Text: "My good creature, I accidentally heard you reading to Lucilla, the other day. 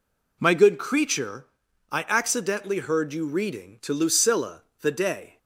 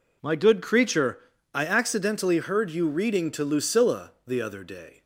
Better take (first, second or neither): second